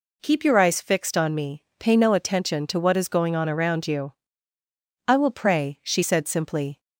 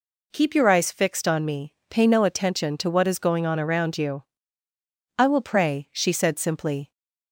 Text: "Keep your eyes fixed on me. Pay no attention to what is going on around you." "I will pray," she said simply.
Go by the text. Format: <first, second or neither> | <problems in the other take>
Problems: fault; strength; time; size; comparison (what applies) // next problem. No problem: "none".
neither | none